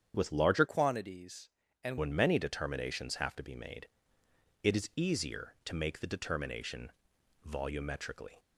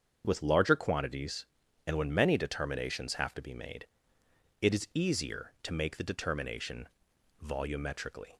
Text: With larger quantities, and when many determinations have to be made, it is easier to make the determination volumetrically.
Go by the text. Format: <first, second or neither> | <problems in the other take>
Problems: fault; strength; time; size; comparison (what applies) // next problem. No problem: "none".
second | starts louder than the rest; strong; until 1.1 s; 8 dB; strong in the second // changes voice from "quantities" to "and"; from 0.6 to 1.9 s; 1.3 s long // pauses between "determination" and "volumetrically"; noticeable; at 6.9 s; 0.56 s long; noticeable in the second